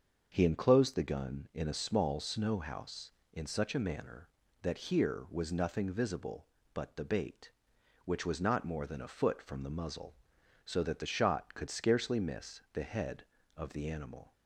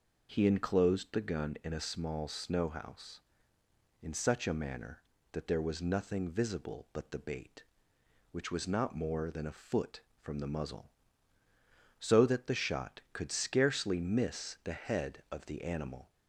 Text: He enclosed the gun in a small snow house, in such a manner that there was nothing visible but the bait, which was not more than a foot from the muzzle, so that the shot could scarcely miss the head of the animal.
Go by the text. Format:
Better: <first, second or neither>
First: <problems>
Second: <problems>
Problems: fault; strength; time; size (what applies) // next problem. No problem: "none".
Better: second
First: starts louder than the rest; until 1.3 s; 6.5 dB // says "here" for "there"; at 4.9 s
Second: none